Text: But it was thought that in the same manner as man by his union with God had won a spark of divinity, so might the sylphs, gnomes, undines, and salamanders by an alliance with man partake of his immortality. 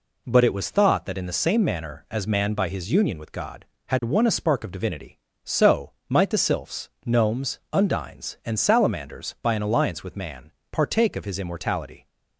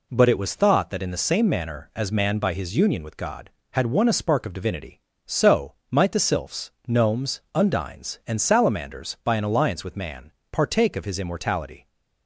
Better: neither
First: pauses between "so" and "might"; slight; at 5.9 s; 0.18 s long // pauses between "man" and "partake"; slight; at 10.5 s; 0.20 s long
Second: pauses between "so" and "might"; slight; at 5.7 s; 0.18 s long // pauses between "man" and "partake"; slight; at 10.3 s; 0.20 s long

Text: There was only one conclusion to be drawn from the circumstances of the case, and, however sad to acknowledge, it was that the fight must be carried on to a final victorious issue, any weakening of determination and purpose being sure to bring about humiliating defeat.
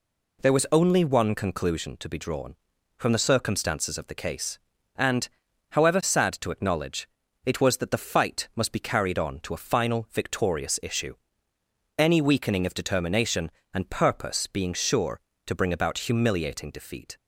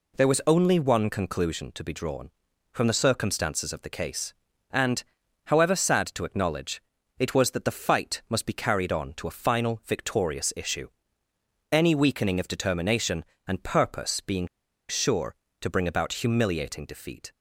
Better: first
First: none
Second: pauses between "being" and "sure"; at 14.4 s; 0.42 s long

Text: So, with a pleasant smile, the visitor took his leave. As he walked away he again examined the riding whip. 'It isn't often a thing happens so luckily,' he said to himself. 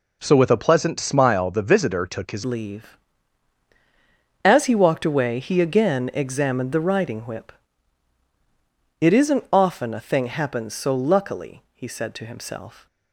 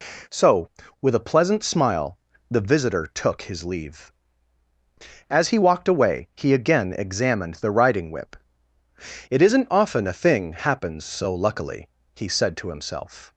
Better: second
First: changes voice at "leave"; from 2.4 s on; 10.4 s long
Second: none

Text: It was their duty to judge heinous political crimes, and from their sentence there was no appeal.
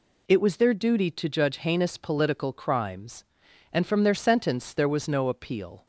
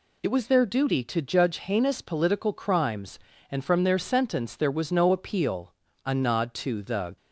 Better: first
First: none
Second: goes on to say "A nod to the"; noticeable; from 6.0 s on; 1.1 s long

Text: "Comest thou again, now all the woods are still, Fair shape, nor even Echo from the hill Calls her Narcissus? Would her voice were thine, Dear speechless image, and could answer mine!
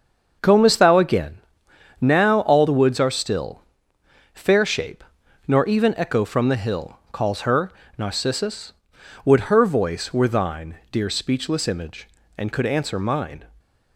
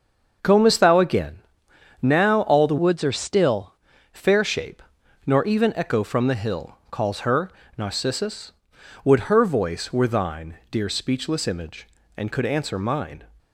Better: first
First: starts louder than the rest; until 2.0 s; 6.5 dB // pauses between "her" and "Narcissus"; slight; at 7.7 s; 0.26 s long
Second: starts louder than the rest; until 2.0 s; 6.5 dB // changes voice from "woods" to "still"; from 2.7 to 3.7 s; 1.0 s long // pauses between "her" and "Narcissus"; slight; at 7.5 s; 0.26 s long

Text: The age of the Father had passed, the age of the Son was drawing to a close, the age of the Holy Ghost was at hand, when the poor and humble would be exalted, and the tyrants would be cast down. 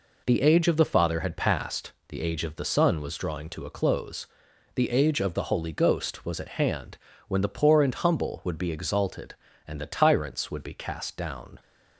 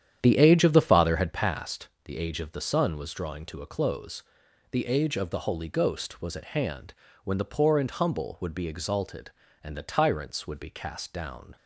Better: first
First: none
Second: starts louder than the rest; strong; until 1.4 s; 9.5 dB

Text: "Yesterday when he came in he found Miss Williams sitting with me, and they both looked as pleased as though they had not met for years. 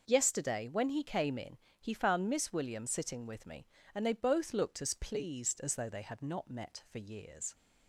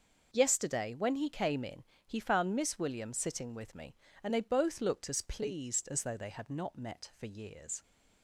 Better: neither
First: pauses between "in" and "he"; slight; at 1.5 s; 0.24 s long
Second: pauses between "in" and "he"; slight; at 1.8 s; 0.24 s long

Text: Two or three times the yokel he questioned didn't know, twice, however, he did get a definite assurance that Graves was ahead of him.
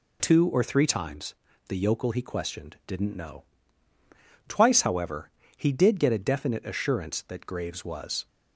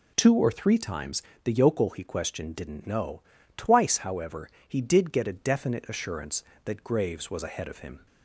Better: second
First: pauses between "times" and "the"; slight; at 1.3 s; 0.34 s long // stops before "ahead of him"; at 8.2 s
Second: pauses between "times" and "the"; slight; at 1.2 s; 0.22 s long

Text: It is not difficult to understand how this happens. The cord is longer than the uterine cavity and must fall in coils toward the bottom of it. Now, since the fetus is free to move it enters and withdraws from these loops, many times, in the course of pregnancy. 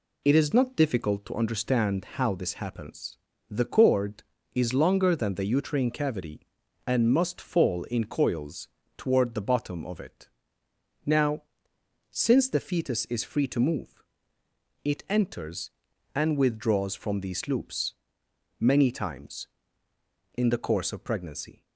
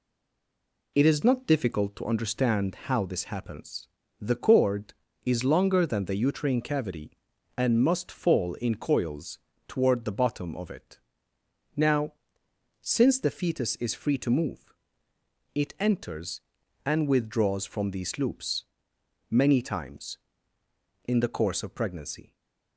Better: first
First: pauses between "coils" and "toward"; slight; at 8.6 s; 0.30 s long // pauses between "move" and "it"; noticeable; at 14.0 s; 0.80 s long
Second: stays silent before the first word; slight; until 0.9 s; 0.9 s long // pauses between "coils" and "toward"; slight; at 9.3 s; 0.30 s long // pauses between "move" and "it"; noticeable; at 14.7 s; 0.80 s long // stays silent after the last word; slight; from 22.2 s on; 0.5 s long

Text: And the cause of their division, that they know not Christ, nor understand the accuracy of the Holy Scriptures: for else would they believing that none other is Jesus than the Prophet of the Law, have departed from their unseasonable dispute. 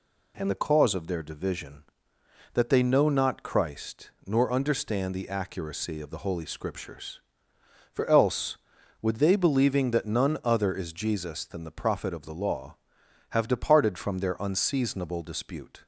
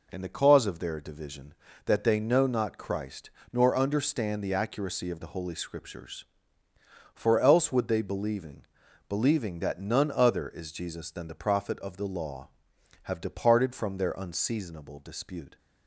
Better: first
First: none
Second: says "believing" twice; at 9.0 s

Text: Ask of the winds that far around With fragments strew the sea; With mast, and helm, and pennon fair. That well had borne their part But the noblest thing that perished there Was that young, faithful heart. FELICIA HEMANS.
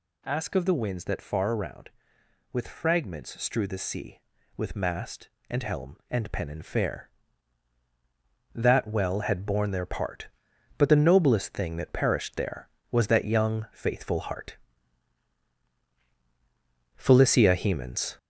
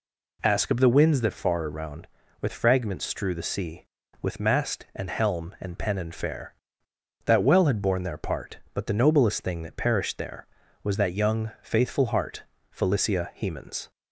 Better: second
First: gets louder; noticeable; throughout; 5 dB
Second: none

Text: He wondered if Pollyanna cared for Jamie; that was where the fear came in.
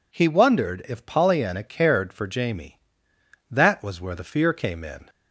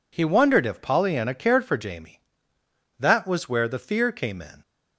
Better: neither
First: none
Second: none

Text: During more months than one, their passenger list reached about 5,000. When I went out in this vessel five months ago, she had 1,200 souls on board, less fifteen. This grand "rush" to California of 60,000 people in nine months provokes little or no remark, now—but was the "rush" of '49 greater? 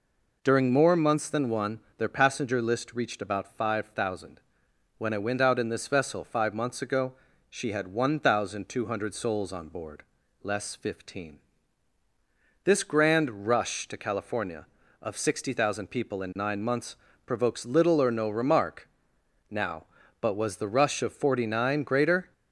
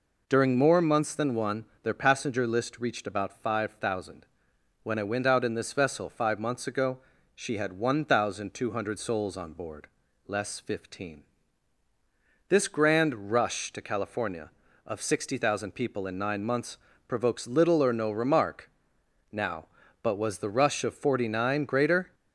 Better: neither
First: pauses between "months" and "provokes"; slight; at 16.9 s; 0.28 s long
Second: pauses between "months" and "provokes"; slight; at 16.7 s; 0.28 s long

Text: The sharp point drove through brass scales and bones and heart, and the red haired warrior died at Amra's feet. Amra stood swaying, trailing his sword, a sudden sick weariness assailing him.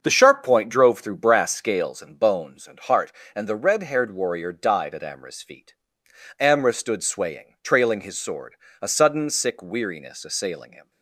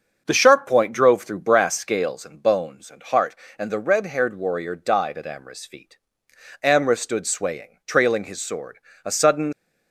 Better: first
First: starts louder than the rest; until 1.0 s; 6.5 dB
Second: starts louder than the rest; until 1.2 s; 6.5 dB // stops before "sick weariness assailing him"; at 9.5 s

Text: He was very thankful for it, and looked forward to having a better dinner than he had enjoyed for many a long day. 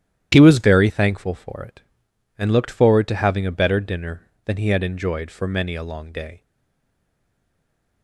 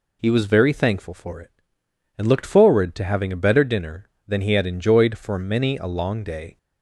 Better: second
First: starts louder than the rest; strong; until 1.3 s; 11 dB // stays silent after the last word; noticeable; from 6.4 s on; 1.6 s long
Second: none

